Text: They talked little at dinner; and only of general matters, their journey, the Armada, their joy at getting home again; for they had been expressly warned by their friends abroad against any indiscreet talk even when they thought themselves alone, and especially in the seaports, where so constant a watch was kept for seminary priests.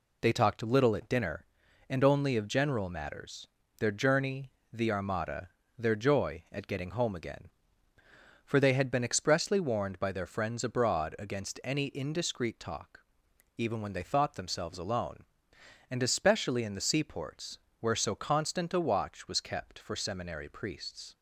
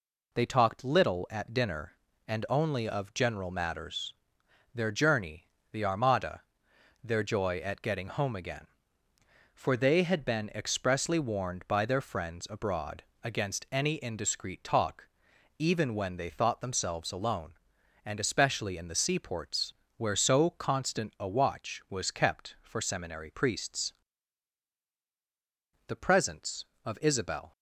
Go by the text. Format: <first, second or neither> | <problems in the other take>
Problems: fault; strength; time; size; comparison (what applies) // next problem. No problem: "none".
first | pauses between "abroad" and "against"; slight; at 13.0 s; 0.22 s long // pauses between "talk" and "even"; noticeable; at 15.0 s; 0.52 s long; noticeable in the first // goes on to say "The presence of Isabel"; from 25.8 s on; 1.6 s long